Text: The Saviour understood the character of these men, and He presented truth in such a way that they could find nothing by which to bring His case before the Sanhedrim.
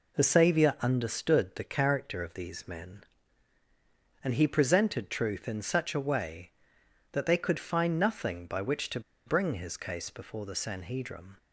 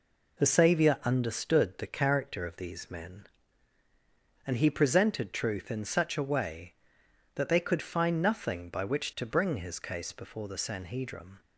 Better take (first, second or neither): second